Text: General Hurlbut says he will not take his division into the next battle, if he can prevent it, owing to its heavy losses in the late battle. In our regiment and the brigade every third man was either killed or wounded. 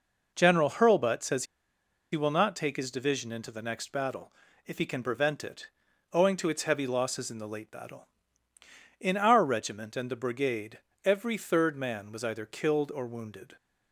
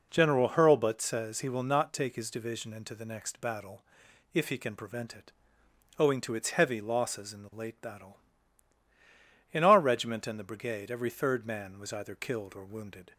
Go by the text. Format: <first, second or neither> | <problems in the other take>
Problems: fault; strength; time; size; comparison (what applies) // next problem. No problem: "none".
second | pauses between "says" and "he"; noticeable; at 1.4 s; 0.67 s long // pauses between "brigade" and "every"; slight; at 10.7 s; 0.26 s long